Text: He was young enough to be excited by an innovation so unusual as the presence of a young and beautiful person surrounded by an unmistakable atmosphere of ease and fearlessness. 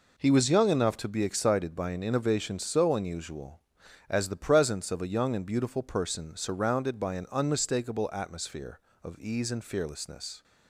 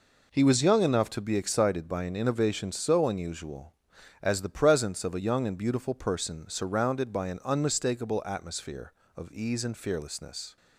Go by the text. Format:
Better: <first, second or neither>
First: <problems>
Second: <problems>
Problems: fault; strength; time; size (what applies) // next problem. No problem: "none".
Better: neither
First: none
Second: none